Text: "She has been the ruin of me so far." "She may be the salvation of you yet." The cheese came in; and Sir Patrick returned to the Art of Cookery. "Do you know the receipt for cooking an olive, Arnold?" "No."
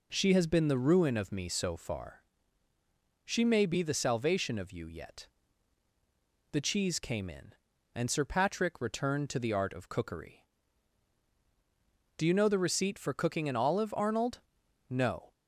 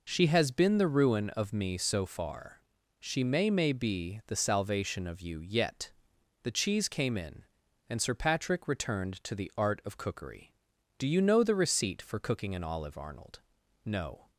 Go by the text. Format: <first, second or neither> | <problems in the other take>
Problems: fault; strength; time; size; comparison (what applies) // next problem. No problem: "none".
first | says "may" twice; at 3.4 s